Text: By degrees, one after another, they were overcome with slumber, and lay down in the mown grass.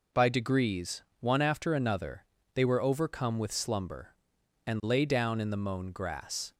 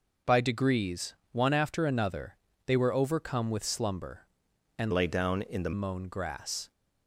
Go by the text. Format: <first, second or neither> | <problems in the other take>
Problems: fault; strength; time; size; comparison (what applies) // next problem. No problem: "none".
first | changes voice from "lay" to "the"; from 4.9 to 5.7 s; 0.8 s long